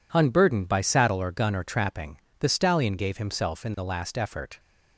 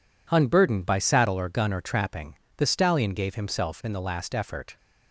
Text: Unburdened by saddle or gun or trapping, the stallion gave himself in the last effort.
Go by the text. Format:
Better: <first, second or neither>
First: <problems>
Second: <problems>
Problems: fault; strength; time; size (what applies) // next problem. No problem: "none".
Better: neither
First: none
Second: none